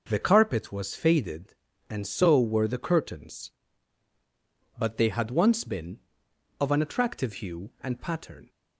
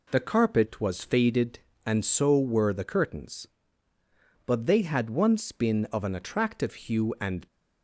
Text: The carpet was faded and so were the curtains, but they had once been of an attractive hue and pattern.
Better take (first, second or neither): first